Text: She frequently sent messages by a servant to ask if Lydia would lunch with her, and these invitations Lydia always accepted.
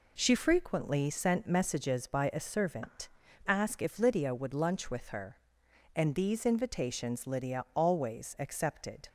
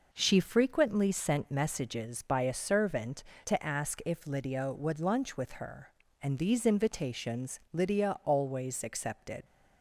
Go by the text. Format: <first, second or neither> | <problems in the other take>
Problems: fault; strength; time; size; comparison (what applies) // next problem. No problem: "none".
second | skips "to"; at 3.2 s